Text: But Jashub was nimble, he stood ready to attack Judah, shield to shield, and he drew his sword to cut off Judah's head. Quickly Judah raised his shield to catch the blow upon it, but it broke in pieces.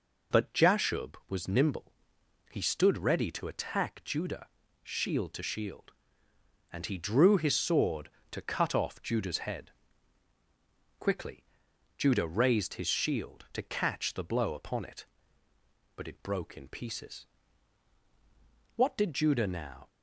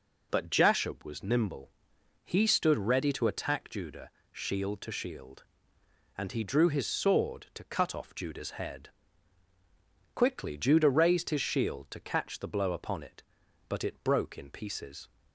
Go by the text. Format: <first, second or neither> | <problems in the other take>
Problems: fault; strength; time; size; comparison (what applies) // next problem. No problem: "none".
second | pauses between "Quickly" and "Judah"; noticeable; at 11.4 s; 0.54 s long // goes on to say "What did Judah now"; noticeable; from 18.7 s on; 1.1 s long